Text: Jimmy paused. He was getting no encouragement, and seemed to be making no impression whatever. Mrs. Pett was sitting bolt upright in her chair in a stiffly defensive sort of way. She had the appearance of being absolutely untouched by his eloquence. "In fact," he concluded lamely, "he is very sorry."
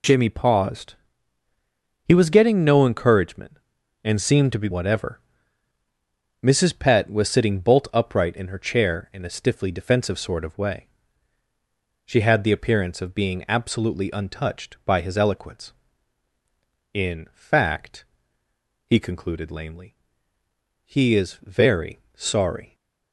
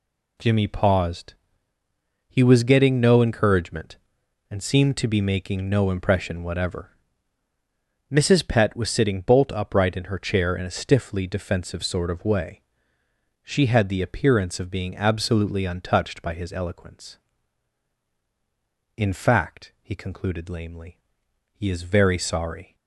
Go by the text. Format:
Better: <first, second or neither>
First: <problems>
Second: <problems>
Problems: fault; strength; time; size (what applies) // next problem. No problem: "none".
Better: second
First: skips "making no impression"; at 4.6 s // pauses between "very" and "sorry"; slight; at 21.9 s; 0.16 s long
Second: none